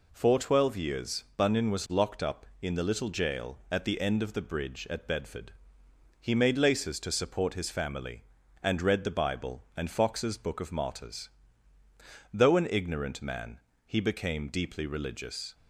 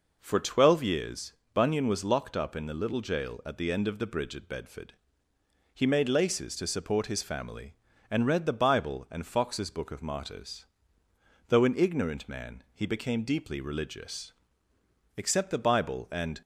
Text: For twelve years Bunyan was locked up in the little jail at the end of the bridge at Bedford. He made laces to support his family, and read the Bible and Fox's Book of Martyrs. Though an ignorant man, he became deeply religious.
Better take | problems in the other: first | pauses between "years" and "Bunyan"; slight; at 1.3 s; 0.21 s long // goes on to say "Except the Bible and"; noticeable; from 15.1 s on; 1.2 s long

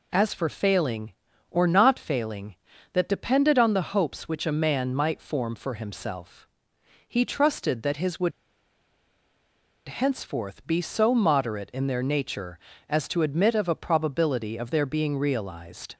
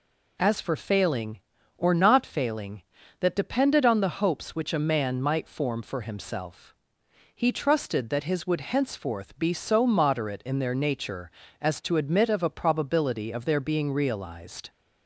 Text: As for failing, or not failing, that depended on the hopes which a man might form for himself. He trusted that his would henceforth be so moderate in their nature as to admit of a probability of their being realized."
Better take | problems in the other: second | pauses between "would" and "henceforth"; strong; at 8.3 s; 1.5 s long

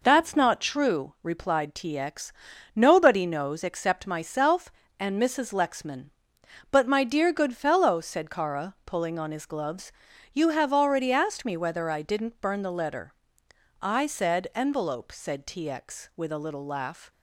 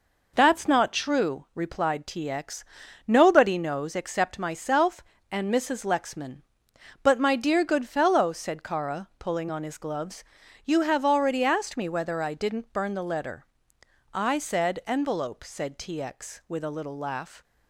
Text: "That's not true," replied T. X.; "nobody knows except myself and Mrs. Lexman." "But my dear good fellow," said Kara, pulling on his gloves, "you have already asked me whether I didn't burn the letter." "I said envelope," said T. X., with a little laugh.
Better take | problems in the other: neither | none

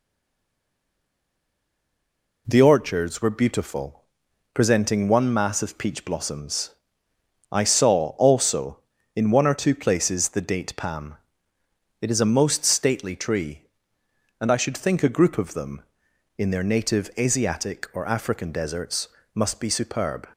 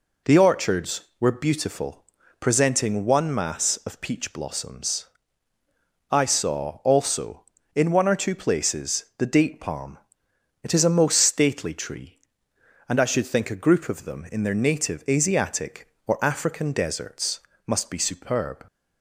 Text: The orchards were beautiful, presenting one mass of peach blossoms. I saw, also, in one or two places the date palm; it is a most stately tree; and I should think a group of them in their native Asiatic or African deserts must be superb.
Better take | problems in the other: second | stays silent before the first word; until 2.4 s; 2.4 s long // pauses between "deserts" and "must"; slight; at 19.0 s; 0.26 s long; slight in the second

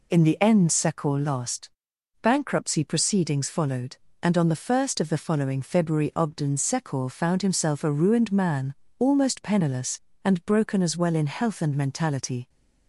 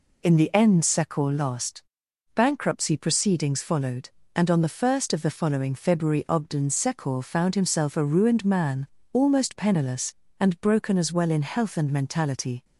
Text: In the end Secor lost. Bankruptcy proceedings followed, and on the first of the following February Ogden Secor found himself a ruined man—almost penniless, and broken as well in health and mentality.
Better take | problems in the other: neither | none

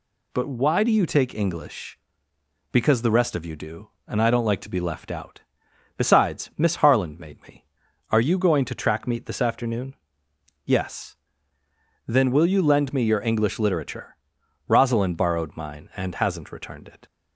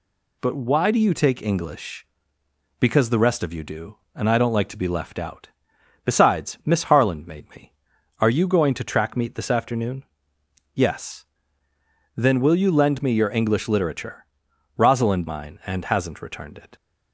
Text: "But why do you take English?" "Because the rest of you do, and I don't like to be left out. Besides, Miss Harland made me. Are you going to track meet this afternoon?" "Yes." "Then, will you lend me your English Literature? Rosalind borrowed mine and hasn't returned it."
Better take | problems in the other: first | skips "borrowed"; at 15.2 s

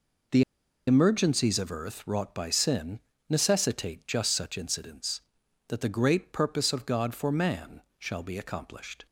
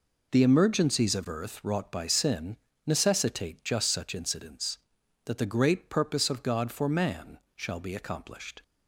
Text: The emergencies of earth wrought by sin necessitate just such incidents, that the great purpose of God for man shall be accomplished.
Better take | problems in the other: second | pauses between "The" and "emergencies"; at 0.4 s; 0.45 s long // pauses between "sin" and "necessitate"; slight; at 2.9 s; 0.28 s long; slight in the second // pauses between "man" and "shall"; slight; at 7.8 s; 0.16 s long; slight in the second

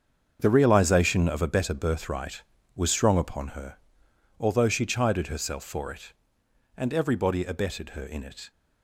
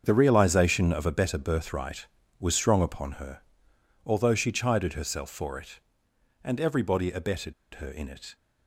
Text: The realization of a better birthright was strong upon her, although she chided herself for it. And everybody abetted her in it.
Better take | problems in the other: first | starts louder than the rest; until 1.0 s; 7 dB; also in the first // pauses between "abetted" and "her"; slight; at 7.5 s; 0.21 s long

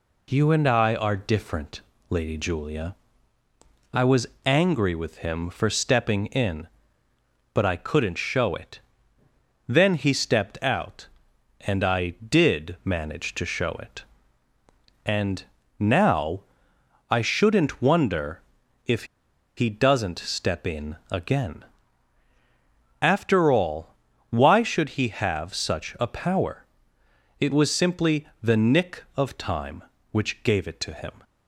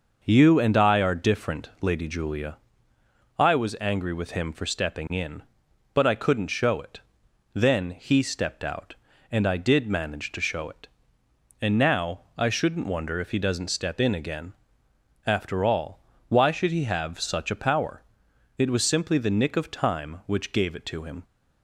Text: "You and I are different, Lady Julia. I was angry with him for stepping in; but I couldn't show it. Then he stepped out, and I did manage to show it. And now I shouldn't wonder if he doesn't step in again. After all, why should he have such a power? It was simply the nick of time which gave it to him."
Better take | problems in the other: second | pauses between "was" and "angry"; slight; at 4.2 s; 0.18 s long // pauses between "And" and "now"; slight; at 15.4 s; 0.34 s long // pauses between "now" and "I"; noticeable; at 16.4 s; 0.68 s long; slight in the second // pauses between "wonder" and "if"; at 18.4 s; 0.42 s long // pauses between "if" and "he"; noticeable; at 19.0 s; 0.51 s long // pauses between "in" and "again"; slight; at 20.9 s; 0.16 s long

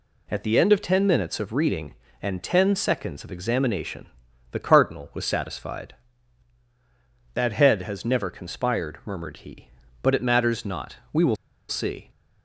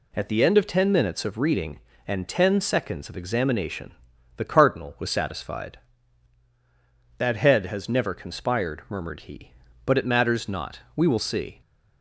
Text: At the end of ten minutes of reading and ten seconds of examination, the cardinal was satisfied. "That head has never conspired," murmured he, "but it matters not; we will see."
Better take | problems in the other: second | pauses between "will" and "see"; slight; at 11.3 s; 0.33 s long

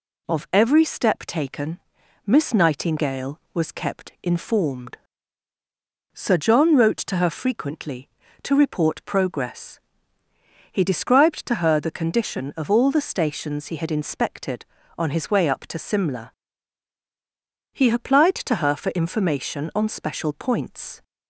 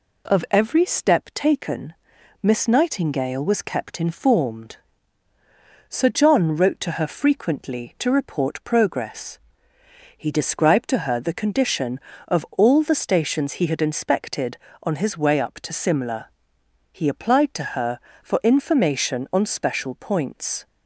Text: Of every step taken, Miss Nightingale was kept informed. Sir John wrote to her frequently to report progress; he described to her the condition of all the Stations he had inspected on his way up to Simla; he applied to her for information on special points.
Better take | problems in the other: neither | none

